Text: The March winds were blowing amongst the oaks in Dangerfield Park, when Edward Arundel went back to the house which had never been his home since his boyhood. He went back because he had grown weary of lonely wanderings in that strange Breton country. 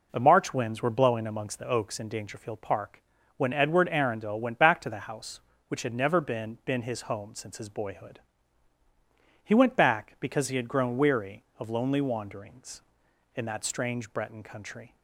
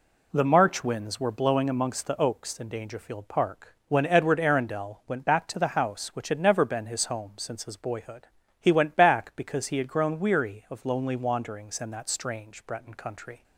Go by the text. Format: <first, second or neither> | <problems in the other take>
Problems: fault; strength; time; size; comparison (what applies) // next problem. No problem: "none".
second | says "been" twice; at 6.6 s